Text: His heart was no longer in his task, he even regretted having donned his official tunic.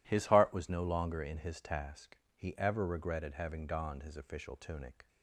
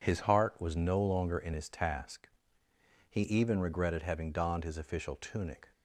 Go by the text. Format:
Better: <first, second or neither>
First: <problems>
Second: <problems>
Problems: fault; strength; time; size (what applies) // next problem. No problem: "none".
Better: second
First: says "ever" for "even"; at 2.5 s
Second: none